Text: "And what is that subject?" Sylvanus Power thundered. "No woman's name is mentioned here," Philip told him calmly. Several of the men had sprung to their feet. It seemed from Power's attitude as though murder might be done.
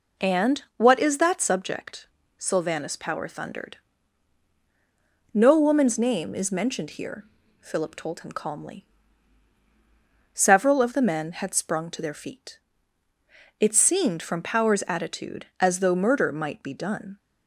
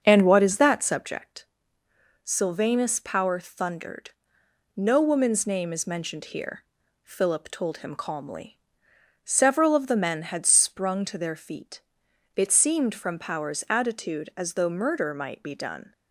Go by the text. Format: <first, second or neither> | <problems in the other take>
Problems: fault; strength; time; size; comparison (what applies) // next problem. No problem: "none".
first | starts louder than the rest; until 1.1 s; 6.5 dB